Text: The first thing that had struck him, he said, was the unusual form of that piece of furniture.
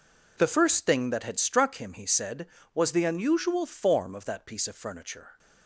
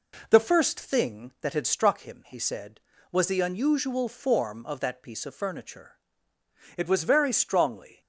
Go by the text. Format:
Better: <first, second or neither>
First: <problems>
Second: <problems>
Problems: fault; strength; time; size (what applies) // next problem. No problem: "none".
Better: first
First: none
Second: goes on to say "It was very strongly"; noticeable; from 6.7 s on; 1.2 s long